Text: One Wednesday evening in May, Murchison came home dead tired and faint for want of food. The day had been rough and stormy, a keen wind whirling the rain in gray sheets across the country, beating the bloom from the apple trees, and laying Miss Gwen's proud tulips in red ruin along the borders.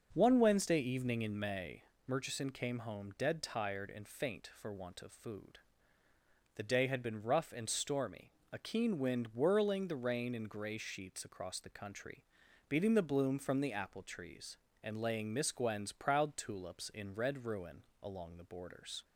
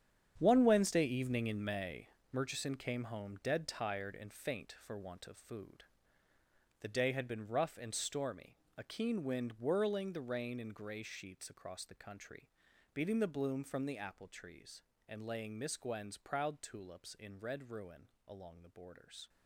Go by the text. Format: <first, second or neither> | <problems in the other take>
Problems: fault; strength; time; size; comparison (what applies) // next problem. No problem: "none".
first | gets quieter; strong; throughout; 12.5 dB // starts louder than the rest; strong; until 1.3 s; 8.5 dB; noticeable in the first // pauses between "ruin" and "along"; slight; at 18.0 s; 0.18 s long; slight in the first